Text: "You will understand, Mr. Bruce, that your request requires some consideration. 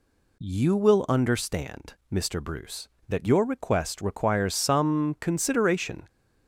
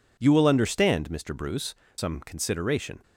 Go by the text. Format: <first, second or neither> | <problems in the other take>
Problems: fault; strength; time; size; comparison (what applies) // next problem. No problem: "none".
first | skips "that your request requires"; at 1.8 s